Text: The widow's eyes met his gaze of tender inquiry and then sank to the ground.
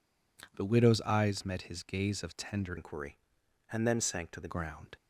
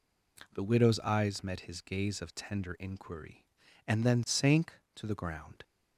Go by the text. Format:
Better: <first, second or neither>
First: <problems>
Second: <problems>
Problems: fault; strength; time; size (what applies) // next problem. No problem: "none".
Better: second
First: changes voice from "inquiry" to "the"; from 2.7 to 4.5 s; 1.8 s long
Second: none